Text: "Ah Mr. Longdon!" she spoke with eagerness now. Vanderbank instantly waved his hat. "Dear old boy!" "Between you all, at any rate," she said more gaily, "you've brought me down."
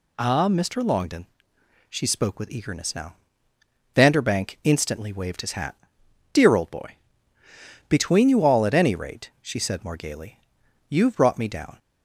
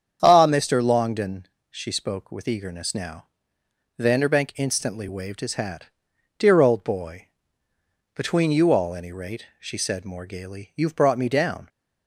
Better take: first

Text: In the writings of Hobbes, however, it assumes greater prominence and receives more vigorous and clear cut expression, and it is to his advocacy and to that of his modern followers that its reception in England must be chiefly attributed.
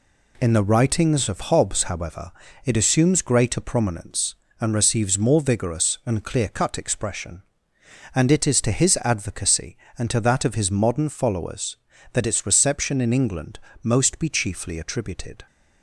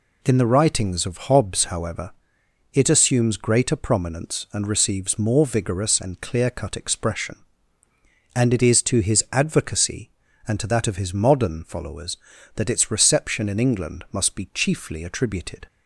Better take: second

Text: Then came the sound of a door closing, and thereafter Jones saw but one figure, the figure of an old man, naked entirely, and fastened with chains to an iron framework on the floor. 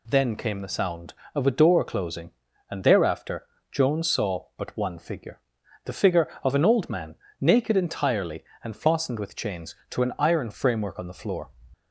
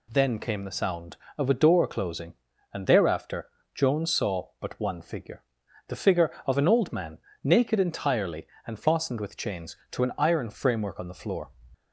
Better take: neither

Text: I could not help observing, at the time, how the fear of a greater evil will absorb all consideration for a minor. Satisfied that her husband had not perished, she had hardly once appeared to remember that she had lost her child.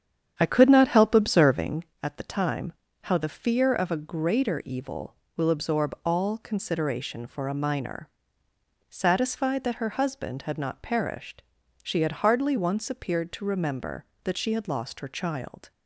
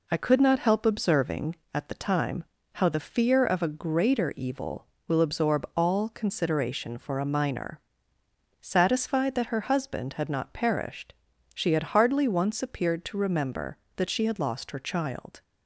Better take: second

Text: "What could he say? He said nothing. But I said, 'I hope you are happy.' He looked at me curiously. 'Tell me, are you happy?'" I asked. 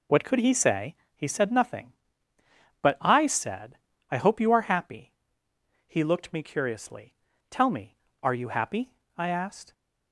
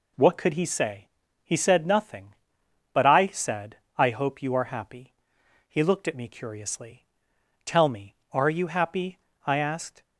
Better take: second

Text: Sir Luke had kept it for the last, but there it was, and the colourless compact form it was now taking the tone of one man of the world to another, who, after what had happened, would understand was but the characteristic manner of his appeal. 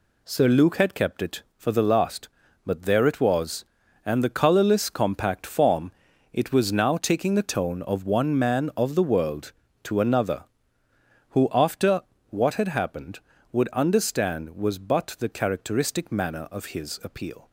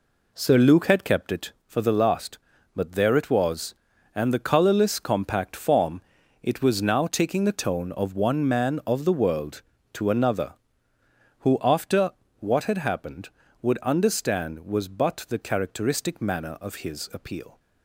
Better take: first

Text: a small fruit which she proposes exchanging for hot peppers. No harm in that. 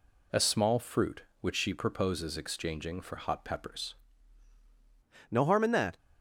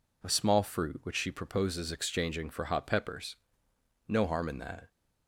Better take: second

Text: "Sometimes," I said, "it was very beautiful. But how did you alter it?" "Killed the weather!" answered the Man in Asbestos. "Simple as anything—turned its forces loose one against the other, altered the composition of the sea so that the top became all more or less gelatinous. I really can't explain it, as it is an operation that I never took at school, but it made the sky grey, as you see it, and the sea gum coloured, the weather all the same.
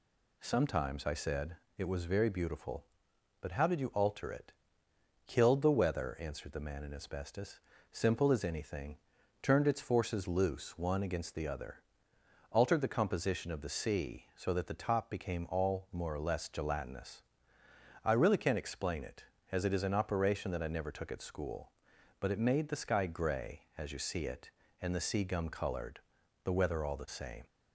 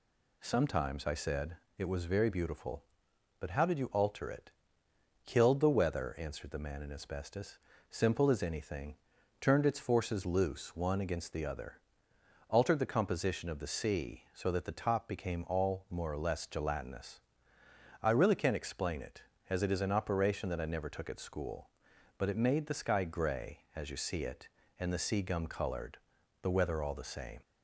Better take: neither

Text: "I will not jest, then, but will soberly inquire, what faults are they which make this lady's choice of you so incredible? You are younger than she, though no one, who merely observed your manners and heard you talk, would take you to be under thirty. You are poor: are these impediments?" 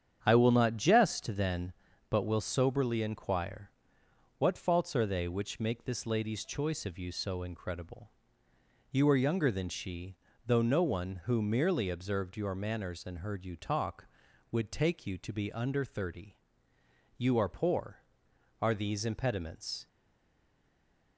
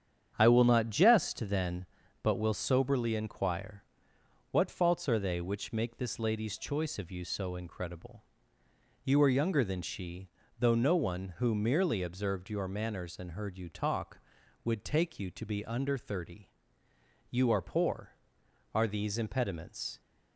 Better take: second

